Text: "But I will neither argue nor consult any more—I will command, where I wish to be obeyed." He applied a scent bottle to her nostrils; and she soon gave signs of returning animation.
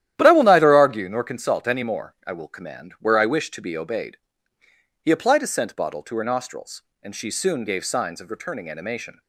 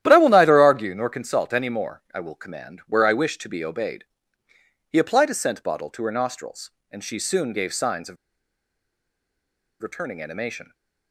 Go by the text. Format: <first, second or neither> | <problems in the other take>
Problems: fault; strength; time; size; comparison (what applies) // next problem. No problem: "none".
first | starts louder than the rest; strong; until 1.0 s; 11.5 dB; strong in the first // pauses between "of" and "returning"; strong; at 8.1 s; 1.6 s long